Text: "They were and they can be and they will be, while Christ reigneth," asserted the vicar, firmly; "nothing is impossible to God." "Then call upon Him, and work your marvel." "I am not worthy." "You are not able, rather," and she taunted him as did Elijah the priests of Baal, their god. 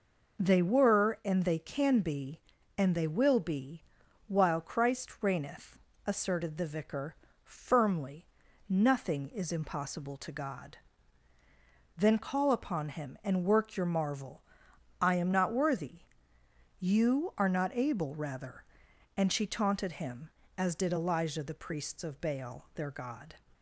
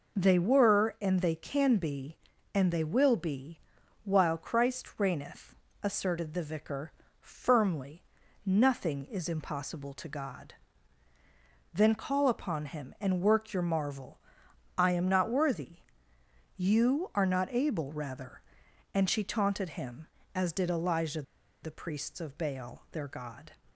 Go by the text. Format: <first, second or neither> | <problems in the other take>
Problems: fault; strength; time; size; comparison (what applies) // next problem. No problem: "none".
first | pauses between "Elijah" and "the"; at 21.2 s; 0.40 s long